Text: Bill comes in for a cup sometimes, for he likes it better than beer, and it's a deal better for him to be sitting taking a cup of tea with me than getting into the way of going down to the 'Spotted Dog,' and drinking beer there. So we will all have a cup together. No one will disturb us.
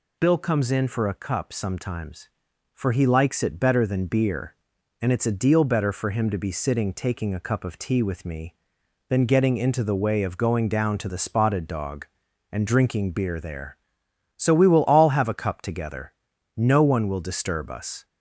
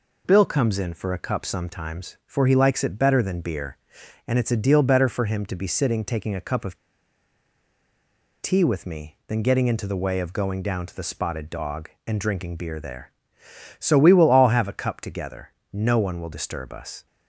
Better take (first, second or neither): first